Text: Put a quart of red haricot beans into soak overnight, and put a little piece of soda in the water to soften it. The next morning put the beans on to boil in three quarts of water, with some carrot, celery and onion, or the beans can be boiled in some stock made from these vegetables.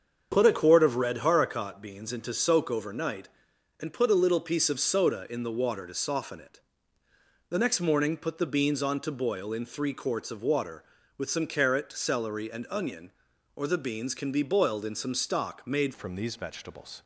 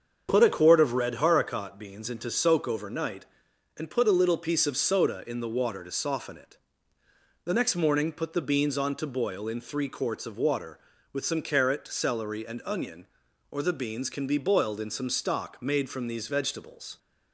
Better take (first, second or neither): second